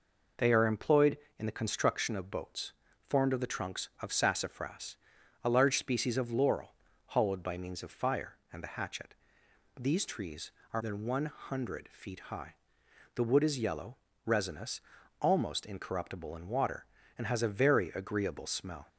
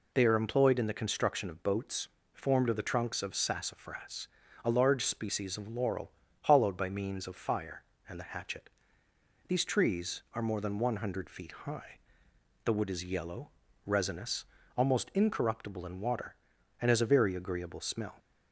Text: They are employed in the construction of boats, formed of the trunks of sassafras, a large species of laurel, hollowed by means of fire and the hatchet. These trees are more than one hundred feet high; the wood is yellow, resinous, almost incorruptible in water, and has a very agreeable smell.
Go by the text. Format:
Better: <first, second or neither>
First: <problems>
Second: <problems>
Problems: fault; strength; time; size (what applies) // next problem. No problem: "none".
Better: second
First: skips "more"; at 10.8 s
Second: none